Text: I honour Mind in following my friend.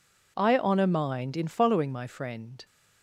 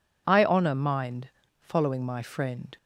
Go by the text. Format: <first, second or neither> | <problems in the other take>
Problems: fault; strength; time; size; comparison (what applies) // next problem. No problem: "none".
first | skips "in"; at 1.4 s